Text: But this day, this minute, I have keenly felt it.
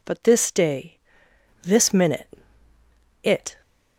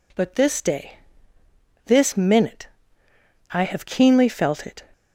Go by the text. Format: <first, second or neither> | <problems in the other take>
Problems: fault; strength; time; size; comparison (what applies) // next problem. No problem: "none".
second | skips "I have keenly felt"; at 2.7 s